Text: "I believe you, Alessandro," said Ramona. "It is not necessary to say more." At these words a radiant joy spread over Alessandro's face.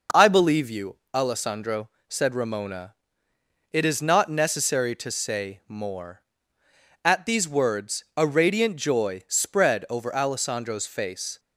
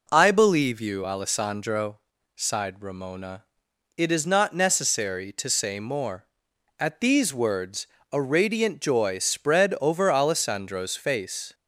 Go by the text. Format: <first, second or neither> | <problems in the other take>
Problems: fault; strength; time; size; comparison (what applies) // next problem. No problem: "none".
first | says "sighed" for "said"; at 2.3 s // pauses between "words" and "a"; slight; at 7.8 s; 0.24 s long